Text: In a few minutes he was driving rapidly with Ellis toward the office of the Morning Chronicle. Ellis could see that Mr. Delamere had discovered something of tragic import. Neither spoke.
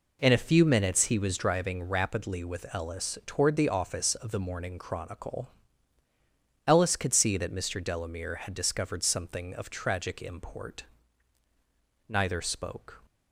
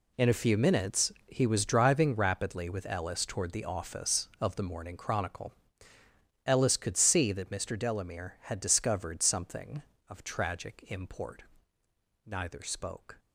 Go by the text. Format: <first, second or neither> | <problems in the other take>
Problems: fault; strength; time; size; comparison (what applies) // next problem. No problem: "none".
first | gets quieter; strong; throughout; 12.5 dB